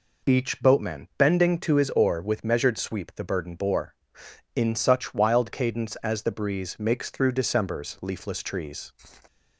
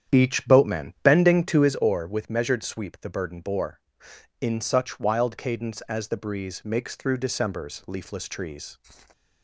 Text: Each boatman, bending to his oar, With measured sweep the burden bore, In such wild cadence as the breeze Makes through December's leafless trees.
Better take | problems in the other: first | starts louder than the rest; strong; until 1.9 s; 9 dB

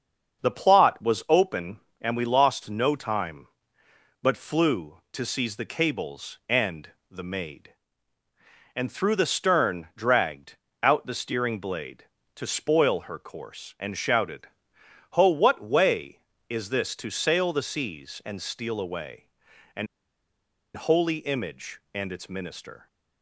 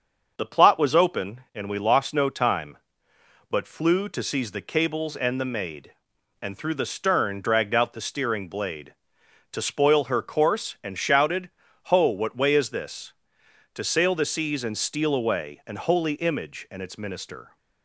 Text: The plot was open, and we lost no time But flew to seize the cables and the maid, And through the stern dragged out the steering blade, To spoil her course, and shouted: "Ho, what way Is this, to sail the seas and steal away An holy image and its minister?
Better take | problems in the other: second | starts louder than the rest; until 1.4 s; 6.5 dB; also in the second // pauses between "and" and "the"; slight; at 6.9 s; 0.20 s long // pauses between "dragged" and "out"; slight; at 10.5 s; 0.26 s long // pauses between "away" and "An"; noticeable; at 19.2 s; 0.48 s long // pauses between "An" and "holy"; noticeable; at 19.8 s; 0.88 s long

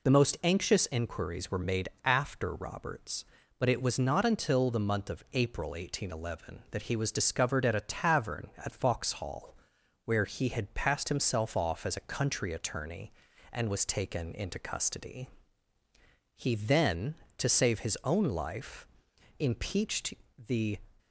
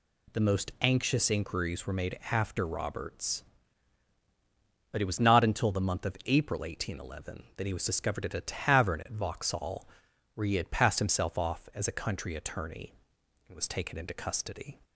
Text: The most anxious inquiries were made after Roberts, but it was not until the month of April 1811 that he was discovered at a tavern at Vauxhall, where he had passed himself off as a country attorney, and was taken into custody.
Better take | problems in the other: second | pauses between "made" and "after"; slight; at 1.8 s; 0.16 s long // goes on to say "He then to save his own life impeached the"; strong; from 16.3 s on; 4.4 s long

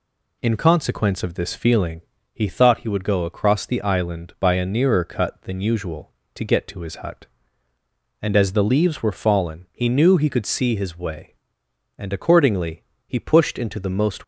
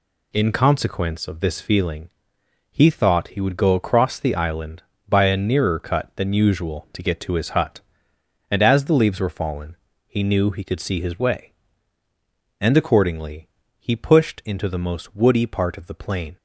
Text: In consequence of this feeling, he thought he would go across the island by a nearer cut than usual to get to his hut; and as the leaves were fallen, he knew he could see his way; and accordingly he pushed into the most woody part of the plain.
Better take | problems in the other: second | pauses between "accordingly" and "he"; slight; at 12.8 s; 0.20 s long; slight in the second // stops before "woody part of the plain"; at 14.2 s

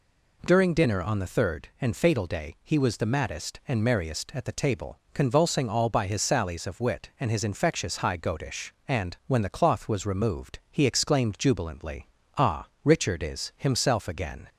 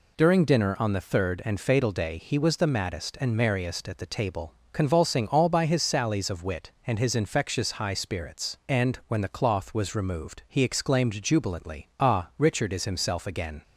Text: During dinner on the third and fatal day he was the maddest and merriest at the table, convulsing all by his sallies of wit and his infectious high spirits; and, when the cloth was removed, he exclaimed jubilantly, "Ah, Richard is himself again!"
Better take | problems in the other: second | says "goatish" for "spirits"; at 8.1 s

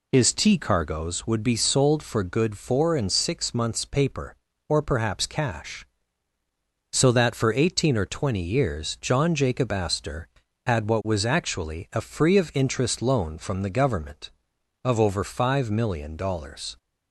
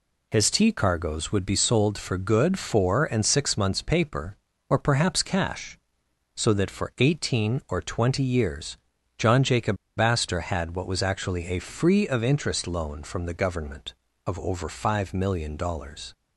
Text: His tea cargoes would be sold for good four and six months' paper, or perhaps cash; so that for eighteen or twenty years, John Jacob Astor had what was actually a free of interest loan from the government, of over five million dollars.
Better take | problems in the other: first | pauses between "Jacob" and "Astor"; slight; at 9.7 s; 0.22 s long

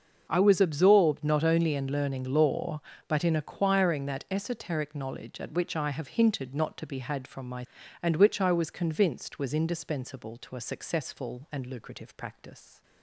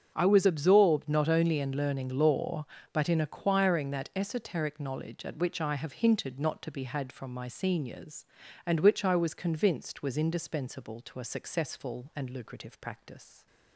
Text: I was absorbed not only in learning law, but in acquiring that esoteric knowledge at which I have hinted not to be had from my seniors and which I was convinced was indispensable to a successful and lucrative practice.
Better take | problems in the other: second | starts louder than the rest; noticeable; until 1.3 s; 6 dB; also in the second // skips "seniors"; at 7.8 s

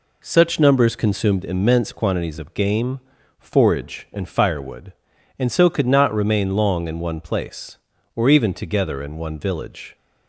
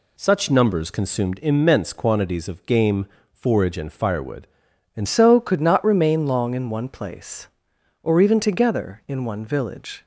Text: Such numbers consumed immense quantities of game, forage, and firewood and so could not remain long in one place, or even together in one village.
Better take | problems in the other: first | changes voice at "so"; from 5.0 s on; 5.0 s long

